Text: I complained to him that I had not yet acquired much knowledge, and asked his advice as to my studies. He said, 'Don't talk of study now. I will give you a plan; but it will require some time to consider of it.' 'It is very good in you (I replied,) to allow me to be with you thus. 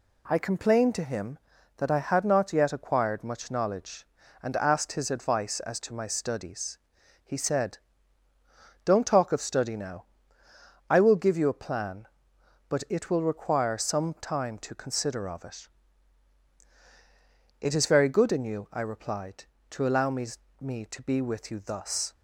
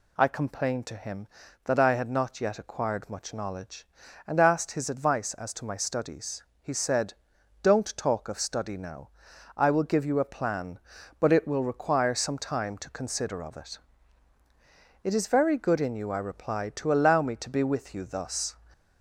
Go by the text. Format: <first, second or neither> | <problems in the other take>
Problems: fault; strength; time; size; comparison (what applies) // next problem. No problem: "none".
second | says "me" twice; at 20.5 s